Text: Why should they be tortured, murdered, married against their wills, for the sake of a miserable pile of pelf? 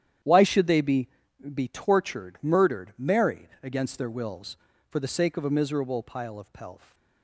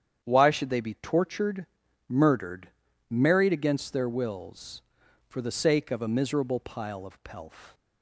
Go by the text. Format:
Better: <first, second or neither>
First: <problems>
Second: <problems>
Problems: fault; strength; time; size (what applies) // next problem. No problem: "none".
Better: second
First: starts louder than the rest; strong; until 1.7 s; 10 dB // says "be" twice; at 1.5 s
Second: starts louder than the rest; strong; until 1.2 s; 9 dB